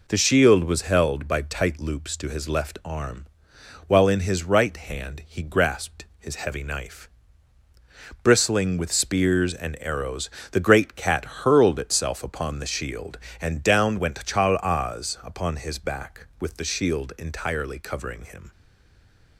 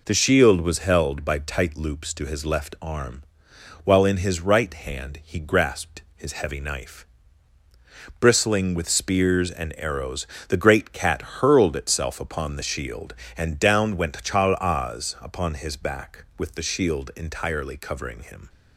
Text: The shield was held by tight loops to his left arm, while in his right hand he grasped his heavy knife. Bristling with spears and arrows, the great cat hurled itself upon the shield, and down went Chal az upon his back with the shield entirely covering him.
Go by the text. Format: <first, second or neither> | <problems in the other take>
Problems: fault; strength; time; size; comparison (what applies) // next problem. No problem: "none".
second | stays silent after the last word; slight; from 18.5 s on; 0.8 s long